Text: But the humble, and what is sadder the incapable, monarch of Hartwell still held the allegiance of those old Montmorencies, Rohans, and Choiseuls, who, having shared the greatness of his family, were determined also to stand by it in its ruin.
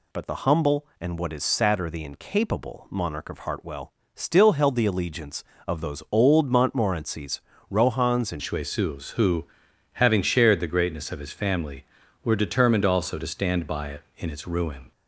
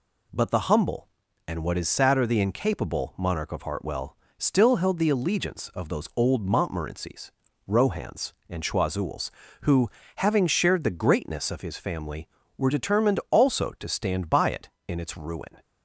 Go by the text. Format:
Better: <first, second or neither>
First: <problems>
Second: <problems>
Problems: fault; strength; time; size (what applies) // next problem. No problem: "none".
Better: second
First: pauses between "Hartwell" and "still"; slight; at 3.9 s; 0.22 s long // changes voice at "Choiseuls"; from 8.4 s on; 6.5 s long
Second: pauses between "Hartwell" and "still"; slight; at 4.1 s; 0.24 s long